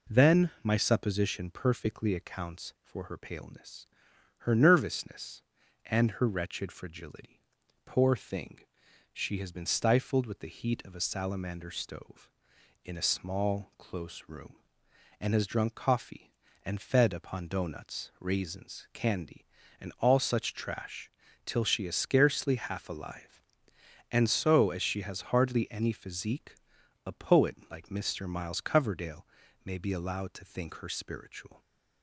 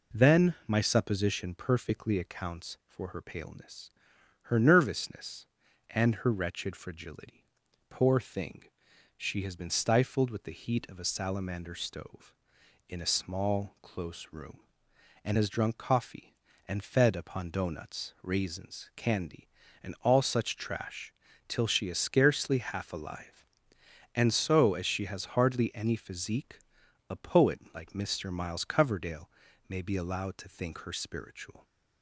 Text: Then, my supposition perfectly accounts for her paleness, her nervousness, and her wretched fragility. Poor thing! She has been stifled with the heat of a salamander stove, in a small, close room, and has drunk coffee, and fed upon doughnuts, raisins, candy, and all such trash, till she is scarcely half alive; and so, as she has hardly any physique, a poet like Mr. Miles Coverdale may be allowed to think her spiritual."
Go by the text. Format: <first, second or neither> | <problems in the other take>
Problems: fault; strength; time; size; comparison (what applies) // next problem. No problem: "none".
neither | pauses between "Coverdale" and "may"; the same in both